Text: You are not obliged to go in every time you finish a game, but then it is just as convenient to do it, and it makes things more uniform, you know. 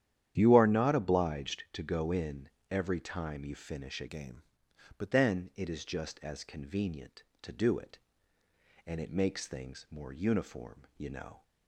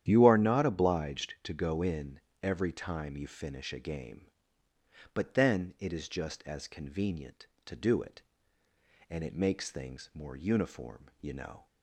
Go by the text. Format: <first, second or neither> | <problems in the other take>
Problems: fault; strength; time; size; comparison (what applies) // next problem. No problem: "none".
second | starts louder than the rest; strong; until 1.3 s; 10.5 dB; strong in the second // pauses between "in" and "every"; slight; at 2.5 s; 0.20 s long; slight in the second // changes voice from "game" to "but"; from 4.0 to 5.1 s; 1.1 s long